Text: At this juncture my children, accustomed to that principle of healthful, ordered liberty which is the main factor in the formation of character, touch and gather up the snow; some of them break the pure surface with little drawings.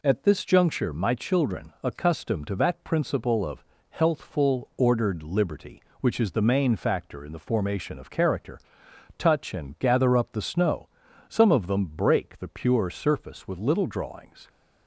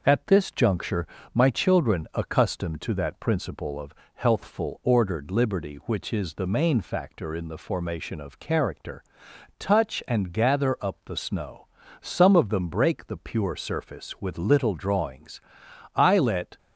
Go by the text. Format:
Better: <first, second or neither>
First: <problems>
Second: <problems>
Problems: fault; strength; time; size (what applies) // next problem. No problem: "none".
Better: first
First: pauses between "of" and "healthful"; slight; at 3.6 s; 0.28 s long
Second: pauses between "juncture" and "my"; slight; at 1.0 s; 0.26 s long // pauses between "of" and "healthful"; slight; at 3.9 s; 0.22 s long // goes on to say "I let"; noticeable; from 15.9 s on; 0.62 s long